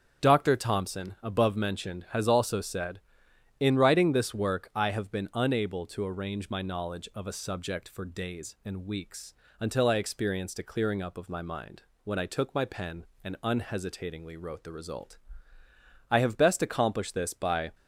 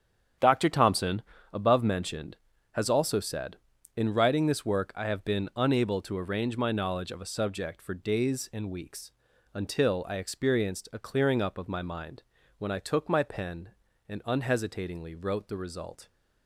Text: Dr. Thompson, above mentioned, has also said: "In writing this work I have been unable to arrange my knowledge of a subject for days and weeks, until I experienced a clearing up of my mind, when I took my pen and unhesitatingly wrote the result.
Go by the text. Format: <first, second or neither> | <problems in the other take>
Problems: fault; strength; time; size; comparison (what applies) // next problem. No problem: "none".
second | starts louder than the rest; strong; until 1.3 s; 8 dB; strong in the second // goes on to say "I have best accomplished this by"; from 16.0 s on; 1.6 s long